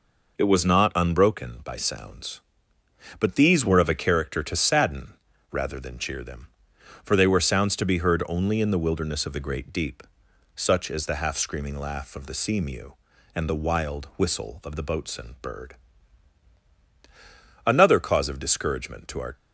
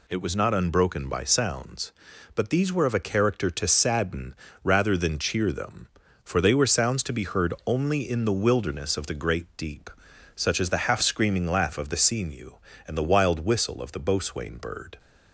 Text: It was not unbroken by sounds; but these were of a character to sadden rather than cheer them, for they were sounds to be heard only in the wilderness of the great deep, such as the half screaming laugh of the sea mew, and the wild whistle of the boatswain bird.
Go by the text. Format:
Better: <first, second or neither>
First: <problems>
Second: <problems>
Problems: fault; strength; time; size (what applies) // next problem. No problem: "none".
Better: second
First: pauses between "sadden" and "rather"; at 5.1 s; 0.38 s long // goes on to say "Another cause of discouragement to our"; strong; from 17.6 s on; 1.7 s long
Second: pauses between "sadden" and "rather"; slight; at 4.3 s; 0.28 s long